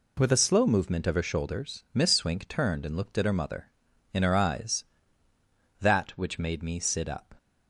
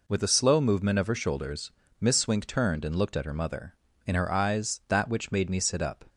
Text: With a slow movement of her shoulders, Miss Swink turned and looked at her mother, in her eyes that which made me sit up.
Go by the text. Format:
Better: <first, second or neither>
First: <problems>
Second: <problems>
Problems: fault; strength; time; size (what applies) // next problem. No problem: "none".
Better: neither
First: none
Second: none